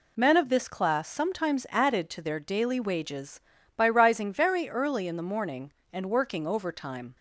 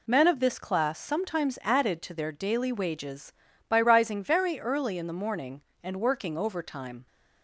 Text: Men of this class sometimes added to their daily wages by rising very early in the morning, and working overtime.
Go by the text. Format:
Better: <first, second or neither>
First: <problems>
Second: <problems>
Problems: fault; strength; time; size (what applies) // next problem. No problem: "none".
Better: neither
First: none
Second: none